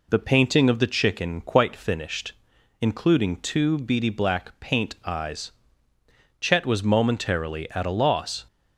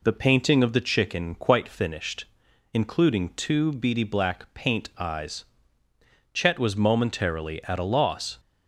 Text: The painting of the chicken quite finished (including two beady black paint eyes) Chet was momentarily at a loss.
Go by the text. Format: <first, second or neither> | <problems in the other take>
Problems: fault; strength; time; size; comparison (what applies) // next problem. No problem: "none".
neither | none